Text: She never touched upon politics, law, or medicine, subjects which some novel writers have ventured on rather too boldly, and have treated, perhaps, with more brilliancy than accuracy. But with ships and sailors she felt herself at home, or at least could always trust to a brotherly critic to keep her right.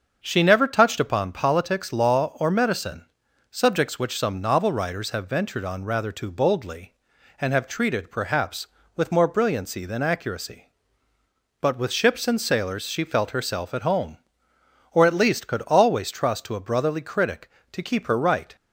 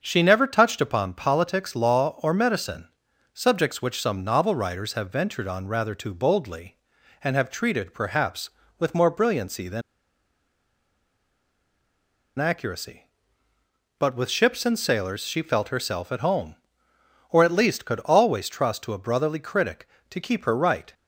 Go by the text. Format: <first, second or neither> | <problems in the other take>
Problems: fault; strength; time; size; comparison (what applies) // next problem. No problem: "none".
first | starts louder than the rest; until 1.0 s; 6.5 dB; also in the first // pauses between "than" and "accuracy"; strong; at 9.8 s; 2.5 s long